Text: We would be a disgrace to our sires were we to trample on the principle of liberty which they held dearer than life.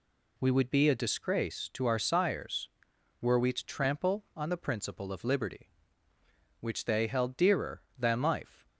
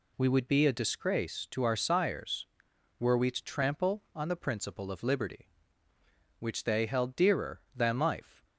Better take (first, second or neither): neither